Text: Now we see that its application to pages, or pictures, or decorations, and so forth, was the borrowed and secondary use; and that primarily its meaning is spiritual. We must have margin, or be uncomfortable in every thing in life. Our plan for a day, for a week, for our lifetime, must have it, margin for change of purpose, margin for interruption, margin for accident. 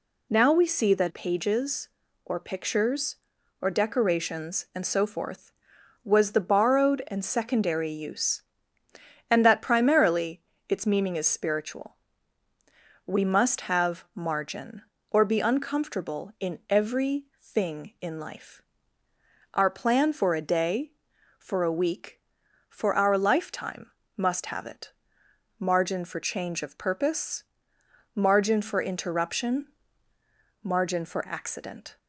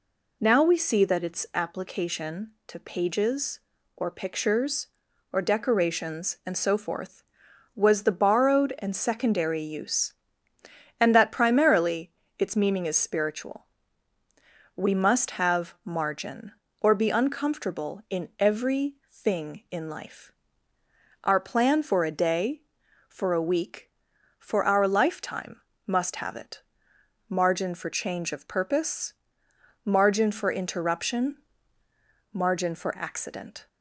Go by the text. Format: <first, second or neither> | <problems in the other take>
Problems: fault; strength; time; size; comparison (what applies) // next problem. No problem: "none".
second | skips "its application to"; at 1.1 s // pauses between "primarily" and "its"; slight; at 10.4 s; 0.26 s long; slight in the second // pauses between "every" and "thing"; slight; at 17.2 s; 0.18 s long; slight in the second